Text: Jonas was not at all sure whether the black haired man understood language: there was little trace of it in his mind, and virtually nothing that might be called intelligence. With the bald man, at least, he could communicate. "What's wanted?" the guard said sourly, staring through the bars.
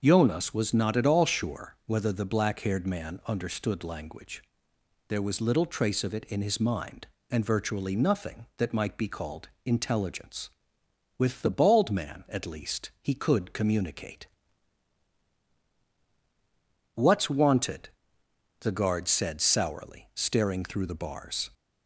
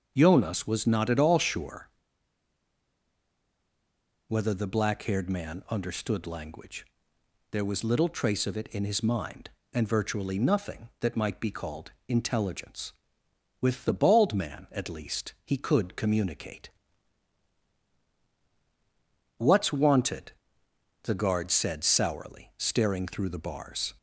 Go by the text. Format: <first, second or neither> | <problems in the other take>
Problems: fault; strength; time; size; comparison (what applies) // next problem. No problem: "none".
first | starts louder than the rest; until 1.1 s; 6.5 dB; also in the first // pauses between "sure" and "whether"; strong; at 1.8 s; 2.4 s long // pauses between "called" and "intelligence"; slight; at 11.9 s; 0.16 s long; slight in the first